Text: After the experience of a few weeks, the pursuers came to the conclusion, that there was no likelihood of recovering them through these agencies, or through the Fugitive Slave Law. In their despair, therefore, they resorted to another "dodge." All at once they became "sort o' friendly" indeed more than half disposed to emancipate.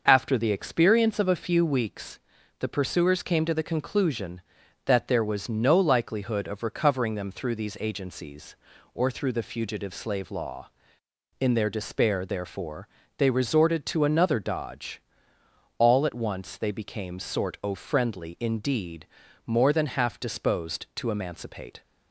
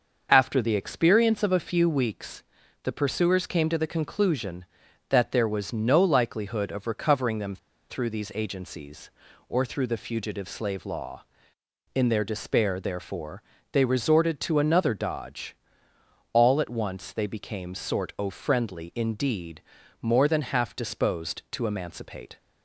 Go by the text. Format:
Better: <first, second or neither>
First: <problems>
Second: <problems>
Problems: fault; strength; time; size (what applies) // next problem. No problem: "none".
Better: first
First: starts louder than the rest; until 1.0 s; 6 dB // pauses between "indeed" and "more"; slight; at 19.0 s; 0.36 s long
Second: starts louder than the rest; until 1.3 s; 6 dB // pauses between "them" and "through"; slight; at 7.5 s; 0.33 s long // pauses between "indeed" and "more"; slight; at 19.6 s; 0.36 s long